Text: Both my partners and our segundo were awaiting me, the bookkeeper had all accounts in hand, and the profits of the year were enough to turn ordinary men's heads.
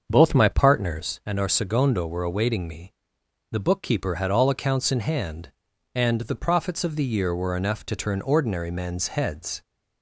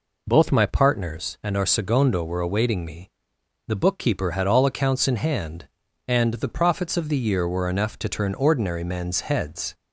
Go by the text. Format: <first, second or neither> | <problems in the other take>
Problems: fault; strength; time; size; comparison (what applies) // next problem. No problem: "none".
second | starts louder than the rest; until 1.2 s; 7 dB